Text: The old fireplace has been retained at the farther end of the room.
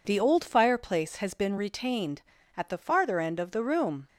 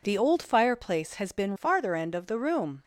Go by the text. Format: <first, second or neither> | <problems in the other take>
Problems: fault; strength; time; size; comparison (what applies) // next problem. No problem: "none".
first | skips "retained at the"; at 1.5 s